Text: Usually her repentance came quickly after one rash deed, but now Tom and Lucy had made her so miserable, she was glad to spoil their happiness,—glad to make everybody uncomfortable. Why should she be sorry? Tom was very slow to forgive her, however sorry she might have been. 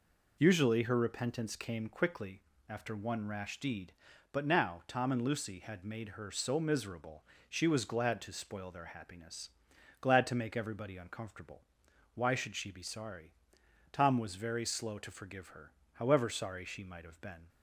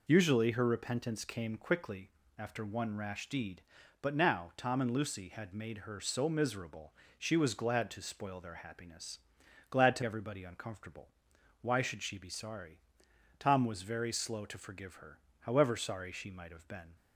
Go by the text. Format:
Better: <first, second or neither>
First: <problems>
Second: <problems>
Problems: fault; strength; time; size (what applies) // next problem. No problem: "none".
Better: first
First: pauses between "quickly" and "after"; slight; at 2.4 s; 0.27 s long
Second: pauses between "quickly" and "after"; slight; at 2.0 s; 0.28 s long // skips "make"; at 10.0 s